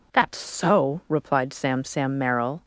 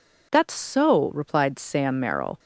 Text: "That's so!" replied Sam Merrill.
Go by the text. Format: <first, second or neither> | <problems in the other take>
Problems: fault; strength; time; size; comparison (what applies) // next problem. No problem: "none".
second | says "Sam" twice; at 1.8 s